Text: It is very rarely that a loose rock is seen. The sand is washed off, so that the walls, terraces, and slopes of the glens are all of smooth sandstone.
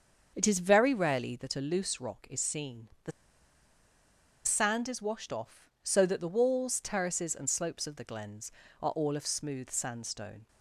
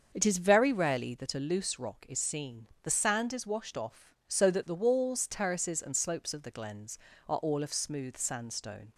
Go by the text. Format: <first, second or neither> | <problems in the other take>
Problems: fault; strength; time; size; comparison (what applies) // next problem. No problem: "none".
second | starts louder than the rest; until 1.3 s; 7 dB; also in the second // pauses between "The" and "sand"; strong; at 3.1 s; 1.3 s long